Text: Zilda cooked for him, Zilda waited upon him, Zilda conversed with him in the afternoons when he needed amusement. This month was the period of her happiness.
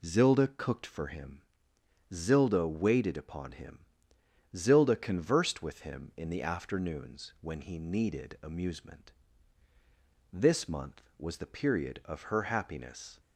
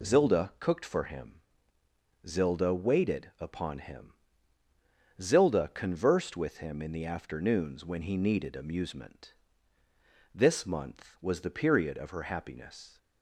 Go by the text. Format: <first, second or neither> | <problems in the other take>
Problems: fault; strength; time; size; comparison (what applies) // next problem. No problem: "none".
neither | none